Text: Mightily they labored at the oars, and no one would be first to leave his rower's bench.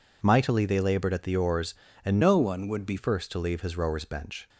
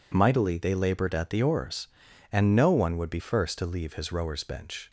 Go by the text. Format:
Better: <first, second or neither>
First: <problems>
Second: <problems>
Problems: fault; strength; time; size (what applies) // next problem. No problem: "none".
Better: second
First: changes voice from "no" to "be"; from 2.2 to 2.9 s; 0.7 s long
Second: none